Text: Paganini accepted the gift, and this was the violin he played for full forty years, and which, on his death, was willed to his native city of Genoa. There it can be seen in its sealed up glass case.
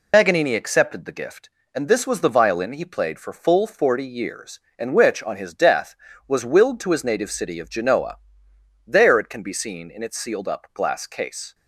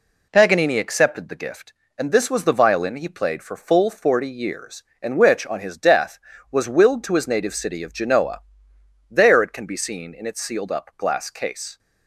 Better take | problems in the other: second | loses the start of "Paganini"; at 0.1 s; 70 ms

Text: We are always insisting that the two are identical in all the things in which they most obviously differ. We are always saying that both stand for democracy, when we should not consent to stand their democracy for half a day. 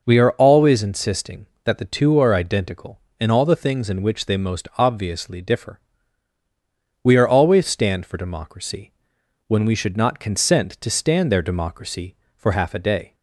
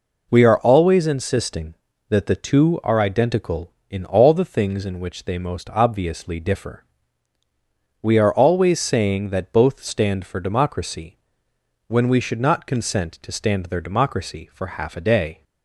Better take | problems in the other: second | skips "saying that both"; at 7.6 s

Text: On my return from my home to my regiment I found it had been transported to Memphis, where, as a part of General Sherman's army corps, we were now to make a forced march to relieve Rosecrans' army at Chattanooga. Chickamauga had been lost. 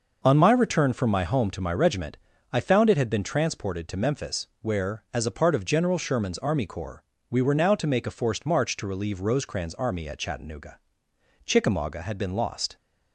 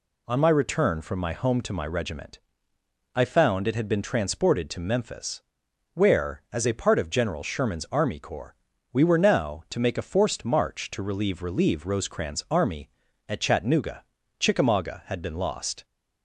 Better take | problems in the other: first | pauses between "regiment" and "I"; noticeable; at 2.3 s; 0.76 s long; slight in the first // says "relieve" twice; at 11.4 s

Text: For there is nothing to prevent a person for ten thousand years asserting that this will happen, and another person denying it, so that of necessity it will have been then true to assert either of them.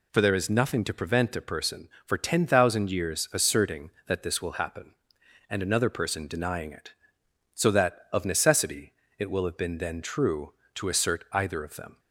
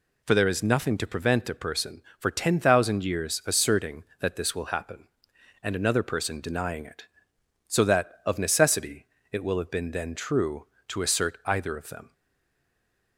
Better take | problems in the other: first | pauses between "necessity" and "it"; slight; at 9.0 s; 0.26 s long; slight in the first // stays silent after the last word; from 12.1 s on; 1.0 s long

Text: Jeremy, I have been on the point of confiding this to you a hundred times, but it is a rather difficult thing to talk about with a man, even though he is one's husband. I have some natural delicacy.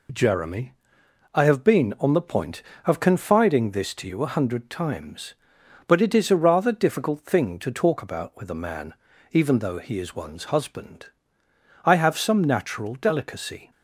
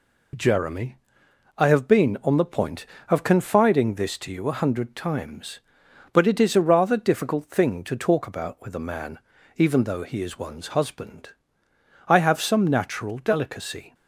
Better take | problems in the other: neither | none

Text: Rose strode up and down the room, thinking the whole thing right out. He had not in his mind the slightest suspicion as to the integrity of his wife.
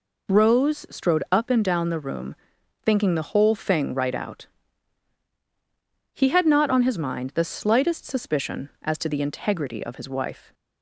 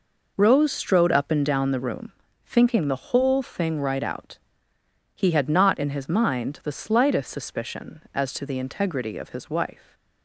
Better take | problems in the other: second | says "on" for "in"; at 6.6 s

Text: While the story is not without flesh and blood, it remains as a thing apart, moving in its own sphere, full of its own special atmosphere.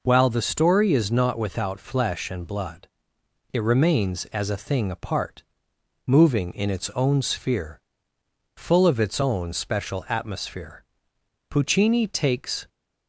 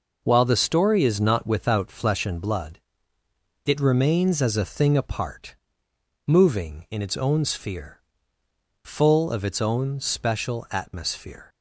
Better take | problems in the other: second | goes on to say "Puccini takes"; noticeable; from 11.5 s on; 1.1 s long

